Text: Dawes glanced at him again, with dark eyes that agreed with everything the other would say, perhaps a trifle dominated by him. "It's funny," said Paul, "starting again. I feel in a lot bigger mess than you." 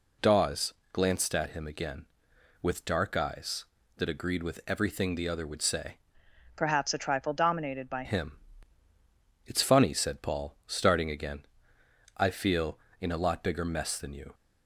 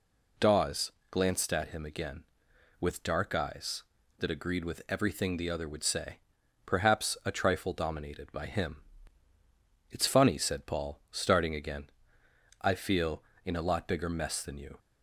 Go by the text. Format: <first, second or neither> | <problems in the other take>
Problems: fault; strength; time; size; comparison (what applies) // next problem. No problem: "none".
second | pauses between "Dawes" and "glanced"; slight; at 0.7 s; 0.20 s long; slight in the second // changes voice from "perhaps" to "by"; from 6.5 to 8.0 s; 1.5 s long